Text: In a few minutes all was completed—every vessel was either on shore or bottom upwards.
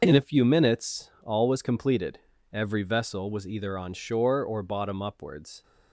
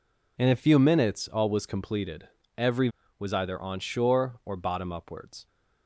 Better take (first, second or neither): first